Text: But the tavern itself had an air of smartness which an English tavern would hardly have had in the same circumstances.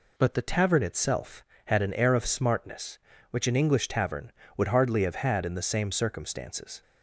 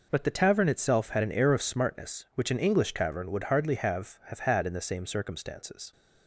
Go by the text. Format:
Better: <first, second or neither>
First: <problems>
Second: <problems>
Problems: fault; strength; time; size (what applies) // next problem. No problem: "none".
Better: first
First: none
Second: says "have" twice; at 4.2 s